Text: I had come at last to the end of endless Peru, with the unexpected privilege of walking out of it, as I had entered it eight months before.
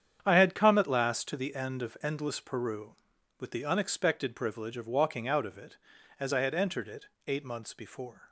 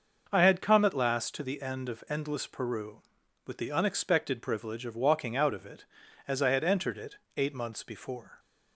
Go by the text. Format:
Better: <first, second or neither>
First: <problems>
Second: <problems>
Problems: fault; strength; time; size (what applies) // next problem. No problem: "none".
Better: second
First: gets quieter; strong; throughout; 11 dB // starts louder than the rest; strong; until 1.2 s; 8.5 dB // pauses between "it" and "eight"; slight; at 7.0 s; 0.22 s long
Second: starts louder than the rest; until 1.3 s; 6 dB // pauses between "it" and "eight"; slight; at 7.1 s; 0.22 s long